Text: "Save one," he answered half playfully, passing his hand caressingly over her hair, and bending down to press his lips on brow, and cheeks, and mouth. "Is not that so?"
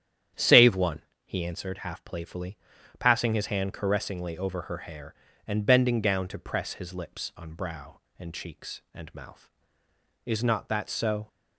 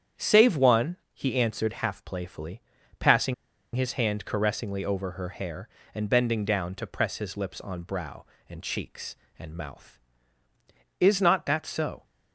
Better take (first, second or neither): first